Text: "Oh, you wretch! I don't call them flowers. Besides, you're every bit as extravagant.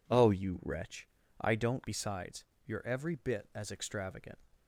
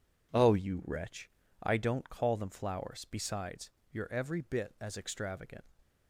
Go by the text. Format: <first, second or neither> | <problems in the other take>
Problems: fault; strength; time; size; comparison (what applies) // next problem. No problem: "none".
second | skips "call them flowers"; at 1.8 s